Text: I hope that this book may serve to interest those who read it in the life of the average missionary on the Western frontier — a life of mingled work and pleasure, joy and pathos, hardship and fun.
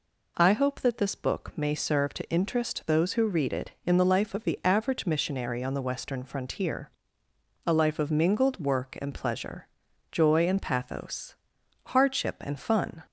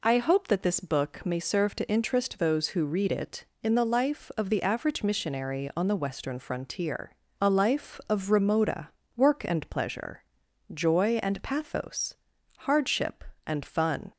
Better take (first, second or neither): first